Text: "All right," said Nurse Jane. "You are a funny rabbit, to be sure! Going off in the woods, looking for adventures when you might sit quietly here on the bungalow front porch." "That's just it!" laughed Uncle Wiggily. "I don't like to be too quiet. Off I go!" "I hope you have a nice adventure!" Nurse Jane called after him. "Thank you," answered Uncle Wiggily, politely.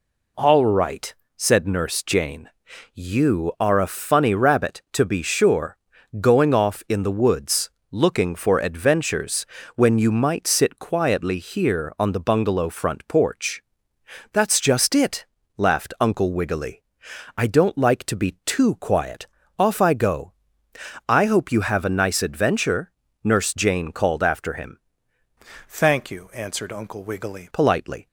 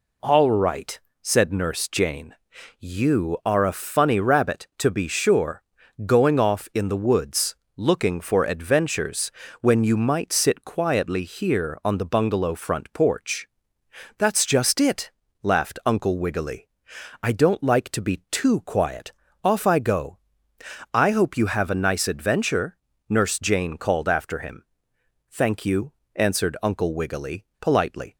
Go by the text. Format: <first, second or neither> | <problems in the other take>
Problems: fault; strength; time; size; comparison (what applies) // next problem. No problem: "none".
second | pauses between "adventures" and "when"; slight; at 9.4 s; 0.30 s long; slight in the second // changes voice from "Thank" to "Wiggily"; from 25.6 to 27.5 s; 1.9 s long